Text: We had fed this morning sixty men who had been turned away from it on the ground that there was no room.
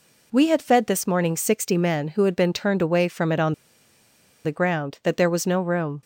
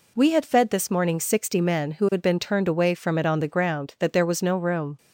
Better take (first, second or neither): second